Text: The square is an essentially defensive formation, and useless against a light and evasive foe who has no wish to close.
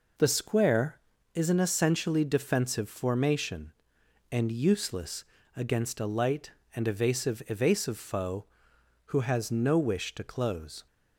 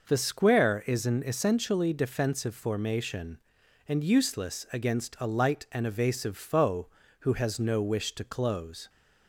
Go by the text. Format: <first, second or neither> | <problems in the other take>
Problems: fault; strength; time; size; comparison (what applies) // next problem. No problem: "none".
second | pauses between "useless" and "against"; slight; at 5.2 s; 0.30 s long // says "evasive" twice; at 7.4 s